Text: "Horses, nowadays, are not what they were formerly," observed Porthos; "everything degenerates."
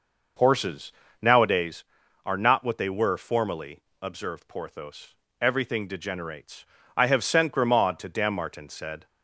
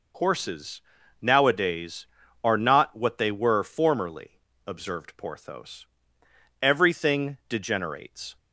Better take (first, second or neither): second